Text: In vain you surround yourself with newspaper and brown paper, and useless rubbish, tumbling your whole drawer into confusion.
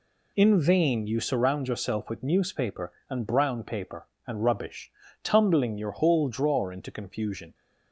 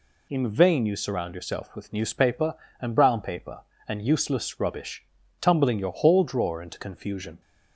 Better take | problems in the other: second | skips "useless"; at 4.4 s

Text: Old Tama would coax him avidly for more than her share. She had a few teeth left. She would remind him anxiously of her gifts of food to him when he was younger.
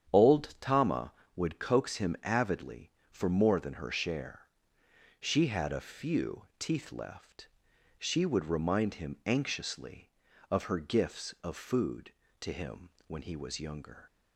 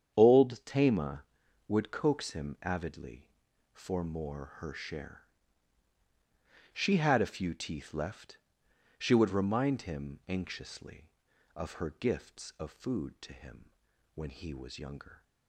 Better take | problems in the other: first | starts louder than the rest; strong; until 1.1 s; 8.5 dB; strong in the first // skips "than"; at 4.5 s // pauses between "him" and "when"; at 13.7 s; 0.42 s long; slight in the first

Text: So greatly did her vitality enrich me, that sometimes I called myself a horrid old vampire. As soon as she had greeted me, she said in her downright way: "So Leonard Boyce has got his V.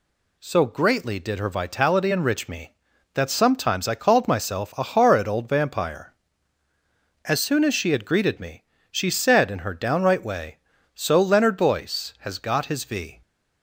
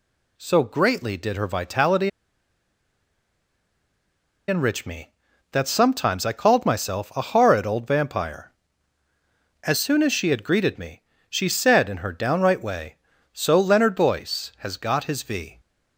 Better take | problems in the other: first | pauses between "vitality" and "enrich"; strong; at 2.0 s; 2.3 s long

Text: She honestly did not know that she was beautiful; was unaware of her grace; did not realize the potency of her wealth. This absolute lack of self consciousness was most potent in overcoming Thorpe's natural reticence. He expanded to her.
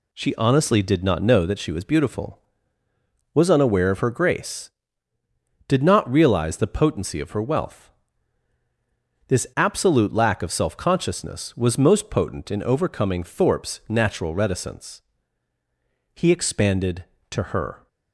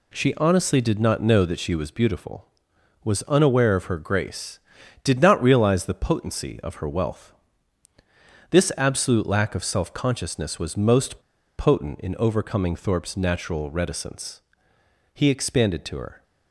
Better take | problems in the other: first | pauses between "most" and "potent"; at 11.1 s; 0.40 s long

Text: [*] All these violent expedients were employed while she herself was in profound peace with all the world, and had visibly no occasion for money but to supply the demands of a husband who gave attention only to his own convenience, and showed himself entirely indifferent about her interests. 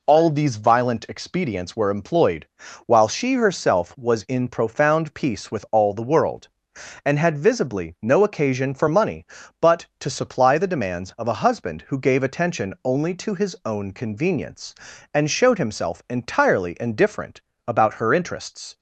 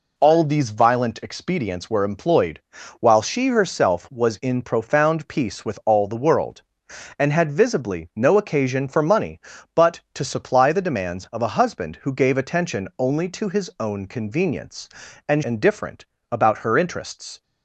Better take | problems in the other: first | pauses between "employed" and "while"; at 2.6 s; 0.38 s long; also in the first // skips "showed himself entirely"; at 15.4 s // pauses between "indifferent" and "about"; slight; at 16.0 s; 0.28 s long; slight in the first

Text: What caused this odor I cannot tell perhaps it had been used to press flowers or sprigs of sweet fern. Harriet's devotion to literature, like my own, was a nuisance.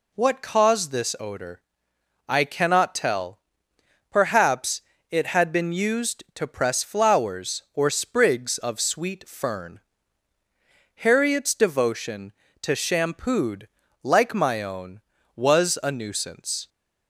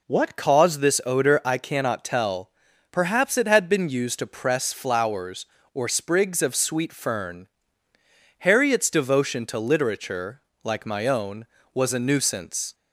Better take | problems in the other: second | pauses between "odor" and "I"; noticeable; at 1.6 s; 0.66 s long // pauses between "tell" and "perhaps"; noticeable; at 3.3 s; 0.72 s long; also in the second // pauses between "perhaps" and "it"; slight; at 4.8 s; 0.28 s long // says "shampooed" for "literature"; at 12.7 s

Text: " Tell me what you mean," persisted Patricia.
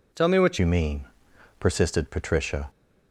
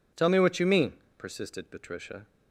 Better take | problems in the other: second | changes voice at "you"; from 0.5 s on; 2.1 s long

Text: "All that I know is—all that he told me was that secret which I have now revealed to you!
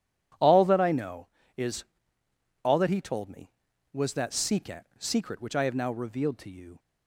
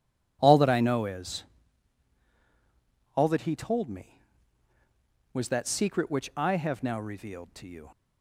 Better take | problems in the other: second | says "secret" twice; at 4.9 s

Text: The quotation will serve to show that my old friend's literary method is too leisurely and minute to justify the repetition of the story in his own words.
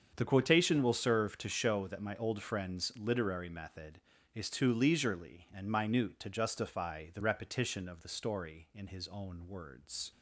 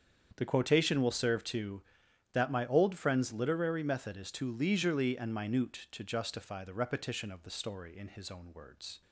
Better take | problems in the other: first | starts louder than the rest; strong; until 1.3 s; 7.5 dB; strong in the first // skips "show"; at 2.0 s

